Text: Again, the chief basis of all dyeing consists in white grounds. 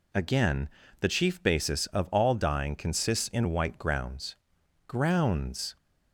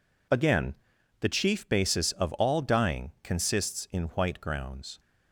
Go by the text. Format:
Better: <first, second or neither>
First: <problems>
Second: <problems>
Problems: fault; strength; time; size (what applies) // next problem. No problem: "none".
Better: second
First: says "grounds" twice; at 4.8 s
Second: none